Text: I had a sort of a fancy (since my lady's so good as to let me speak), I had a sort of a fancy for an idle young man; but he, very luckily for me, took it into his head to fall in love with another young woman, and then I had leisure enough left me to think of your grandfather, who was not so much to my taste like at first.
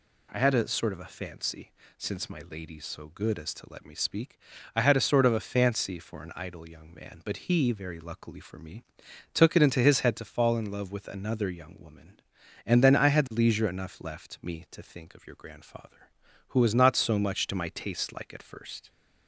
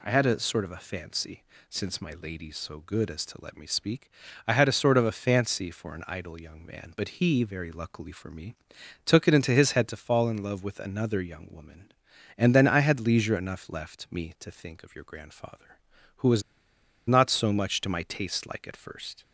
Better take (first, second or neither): first